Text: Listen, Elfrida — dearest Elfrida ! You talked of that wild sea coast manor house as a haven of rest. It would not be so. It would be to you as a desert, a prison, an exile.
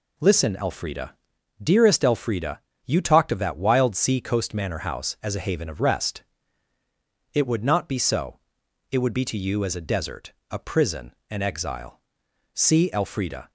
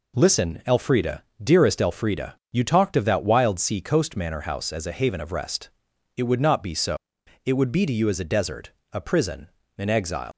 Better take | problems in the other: second | goes on to say "See Elfrida"; noticeable; from 12.5 s on; 0.96 s long

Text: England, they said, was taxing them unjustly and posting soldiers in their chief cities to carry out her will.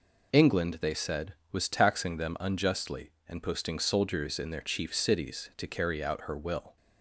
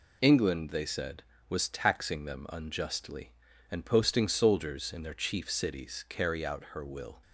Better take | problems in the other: first | skips "to"; at 6.0 s

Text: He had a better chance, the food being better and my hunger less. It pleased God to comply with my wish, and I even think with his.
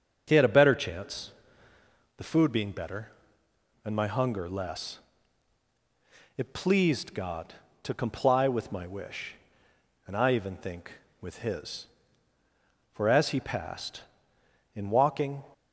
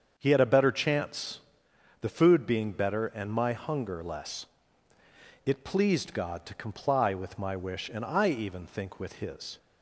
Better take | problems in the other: second | starts louder than the rest; until 1.2 s; 6.5 dB; also in the second // goes on to say "For as he passed in walking"; strong; from 12.9 s on; 2.5 s long

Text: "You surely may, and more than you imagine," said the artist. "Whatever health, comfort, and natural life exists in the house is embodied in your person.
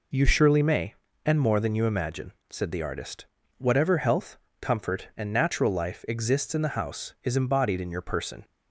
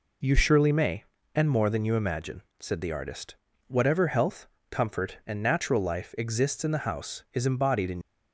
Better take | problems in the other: first | stops before "your person"; at 8.0 s

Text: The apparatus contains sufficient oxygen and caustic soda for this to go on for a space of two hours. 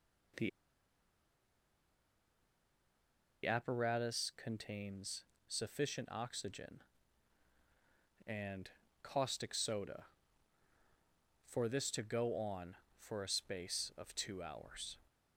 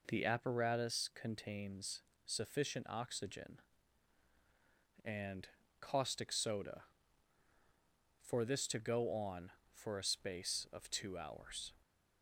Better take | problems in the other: second | pauses between "The" and "apparatus"; strong; at 0.4 s; 2.9 s long // pauses between "contains" and "sufficient"; slight; at 5.2 s; 0.24 s long; slight in the second // pauses between "and" and "caustic"; slight; at 8.6 s; 0.32 s long; slight in the second

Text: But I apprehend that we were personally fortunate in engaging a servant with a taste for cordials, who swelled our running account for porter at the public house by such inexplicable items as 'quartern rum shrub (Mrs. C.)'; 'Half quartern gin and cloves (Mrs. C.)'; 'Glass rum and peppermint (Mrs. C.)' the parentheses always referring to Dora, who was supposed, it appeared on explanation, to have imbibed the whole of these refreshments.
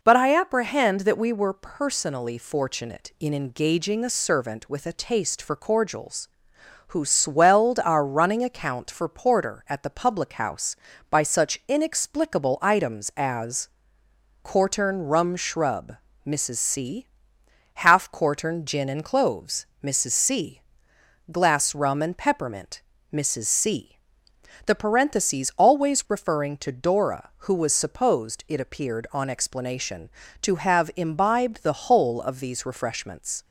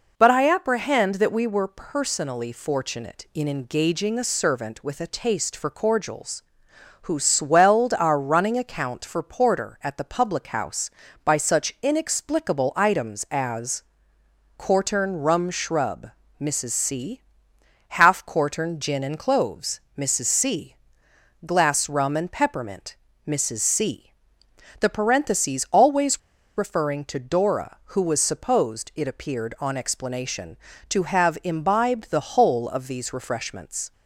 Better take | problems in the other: first | pauses between "as" and "quartern"; noticeable; at 13.8 s; 0.74 s long; noticeable in the first // pauses between "always" and "referring"; at 26.1 s; 0.37 s long

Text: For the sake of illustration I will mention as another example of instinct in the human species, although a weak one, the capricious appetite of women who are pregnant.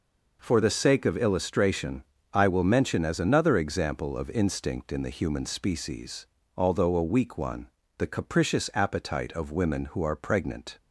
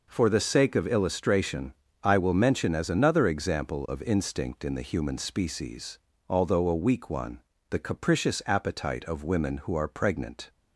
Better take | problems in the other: neither | pauses between "illustration" and "I"; slight; the same in both

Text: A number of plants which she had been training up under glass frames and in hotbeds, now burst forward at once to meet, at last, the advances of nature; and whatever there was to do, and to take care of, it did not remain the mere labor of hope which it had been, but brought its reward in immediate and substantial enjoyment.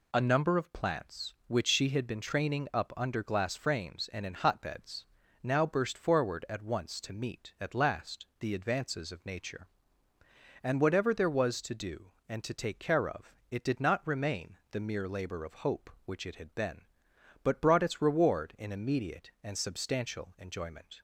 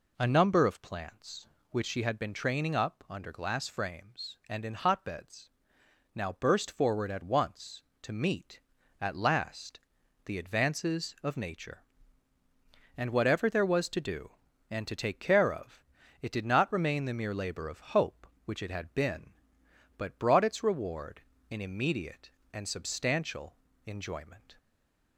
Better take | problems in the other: first | pauses between "substantial" and "enjoyment"; slight; at 23.5 s; 0.32 s long // stays silent after the last word; slight; from 24.5 s on; 0.6 s long

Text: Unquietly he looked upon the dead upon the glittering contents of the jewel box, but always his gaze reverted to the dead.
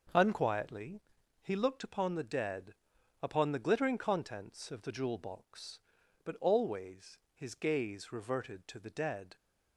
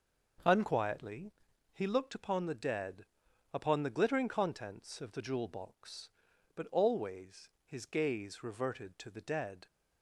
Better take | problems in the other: neither | pauses between "Unquietly" and "he"; the same in both // pauses between "dead" and "upon"; noticeable; the same in both // pauses between "always" and "his"; slight; the same in both

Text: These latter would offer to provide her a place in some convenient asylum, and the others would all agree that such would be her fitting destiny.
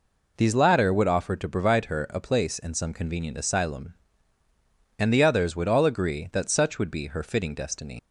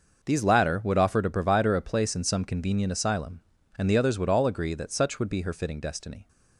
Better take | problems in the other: second | leaves "destiny" unfinished; at 7.9 s; 65 ms

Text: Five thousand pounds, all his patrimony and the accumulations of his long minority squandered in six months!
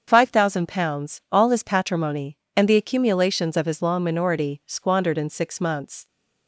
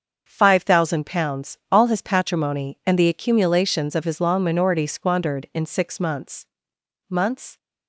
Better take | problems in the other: first | starts louder than the rest; until 1.2 s; 6.5 dB; also in the first // says "months" twice; at 7.0 s

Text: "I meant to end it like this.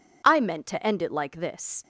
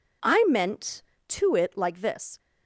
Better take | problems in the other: first | skips "end"; at 1.5 s

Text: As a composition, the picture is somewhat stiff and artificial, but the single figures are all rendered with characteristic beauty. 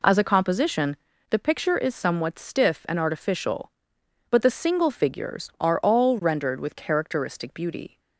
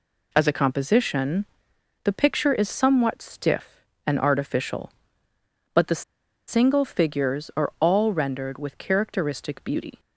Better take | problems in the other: first | pauses between "the" and "single"; noticeable; at 6.0 s; 0.46 s long

